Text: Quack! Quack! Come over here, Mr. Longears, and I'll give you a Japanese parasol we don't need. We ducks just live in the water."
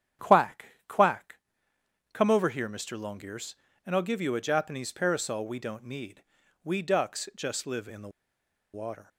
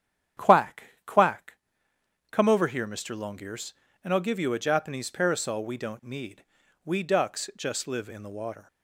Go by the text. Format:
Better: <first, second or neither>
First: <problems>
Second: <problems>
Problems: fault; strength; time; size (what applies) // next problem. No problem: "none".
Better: second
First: starts louder than the rest; strong; until 2.1 s; 9 dB // pauses between "the" and "water"; noticeable; at 8.1 s; 0.64 s long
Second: starts louder than the rest; strong; until 2.3 s; 9 dB